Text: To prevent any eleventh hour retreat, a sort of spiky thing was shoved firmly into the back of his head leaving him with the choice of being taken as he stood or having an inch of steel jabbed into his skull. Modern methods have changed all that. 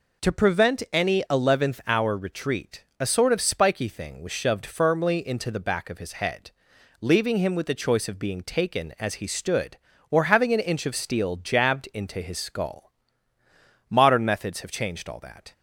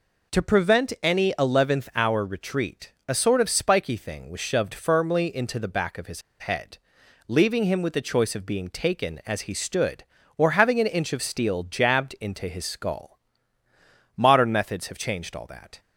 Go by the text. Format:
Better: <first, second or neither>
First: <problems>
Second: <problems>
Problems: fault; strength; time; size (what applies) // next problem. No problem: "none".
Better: first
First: pauses between "head" and "leaving"; noticeable; at 6.5 s; 0.48 s long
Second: pauses between "his" and "head"; slight; at 6.2 s; 0.18 s long // pauses between "head" and "leaving"; noticeable; at 6.7 s; 0.48 s long